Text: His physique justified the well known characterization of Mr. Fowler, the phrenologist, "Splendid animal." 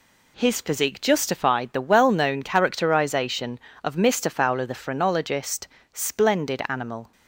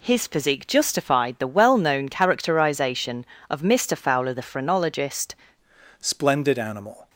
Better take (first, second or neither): first